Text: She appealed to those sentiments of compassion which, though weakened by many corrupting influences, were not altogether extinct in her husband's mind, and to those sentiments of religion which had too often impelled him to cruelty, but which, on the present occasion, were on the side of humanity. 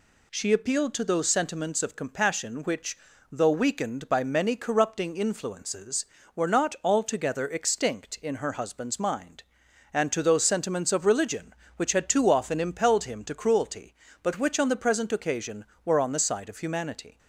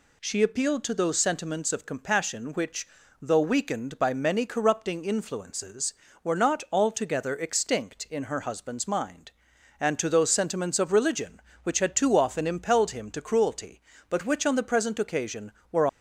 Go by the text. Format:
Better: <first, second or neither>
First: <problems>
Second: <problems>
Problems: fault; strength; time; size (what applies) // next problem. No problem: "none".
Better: first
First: none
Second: stops before "on the side of humanity"; at 15.8 s